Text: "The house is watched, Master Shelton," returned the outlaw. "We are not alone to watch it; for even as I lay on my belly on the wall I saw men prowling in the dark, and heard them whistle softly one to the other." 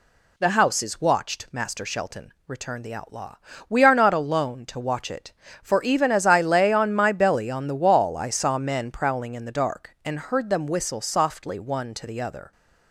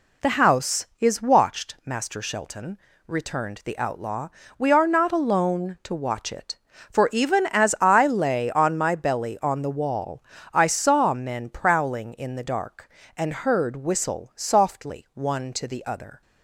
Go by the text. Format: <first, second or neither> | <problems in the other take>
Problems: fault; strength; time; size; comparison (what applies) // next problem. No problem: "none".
first | pauses between "wall" and "I"; slight; at 10.2 s; 0.30 s long // skips "them"; at 13.7 s